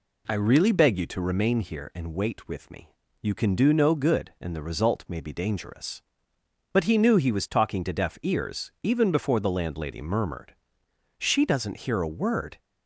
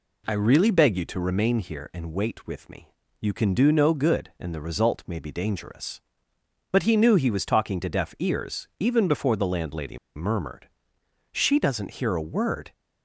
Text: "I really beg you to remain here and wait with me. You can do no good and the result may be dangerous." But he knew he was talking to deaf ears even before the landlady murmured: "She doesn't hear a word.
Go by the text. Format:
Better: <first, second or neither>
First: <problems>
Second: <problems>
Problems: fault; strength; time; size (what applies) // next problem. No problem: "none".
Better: first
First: none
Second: pauses between "landlady" and "murmured"; slight; at 9.9 s; 0.18 s long